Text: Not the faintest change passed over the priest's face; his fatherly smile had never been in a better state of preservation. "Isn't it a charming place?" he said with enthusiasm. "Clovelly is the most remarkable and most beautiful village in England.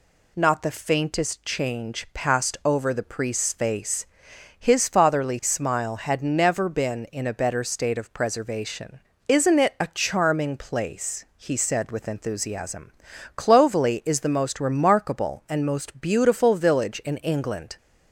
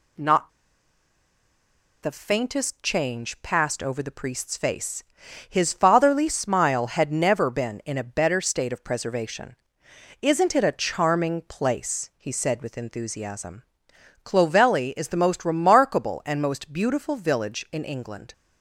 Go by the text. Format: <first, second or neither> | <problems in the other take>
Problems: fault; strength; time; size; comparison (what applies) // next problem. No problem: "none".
first | pauses between "Not" and "the"; strong; at 0.5 s; 1.5 s long